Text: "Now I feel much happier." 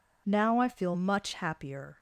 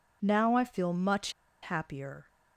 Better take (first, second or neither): first